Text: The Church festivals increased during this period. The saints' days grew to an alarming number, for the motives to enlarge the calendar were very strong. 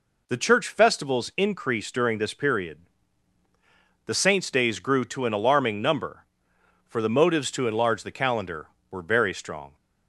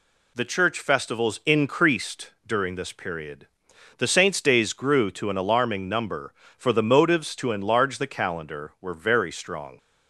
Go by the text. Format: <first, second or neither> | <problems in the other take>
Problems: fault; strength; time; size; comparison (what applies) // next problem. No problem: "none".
neither | none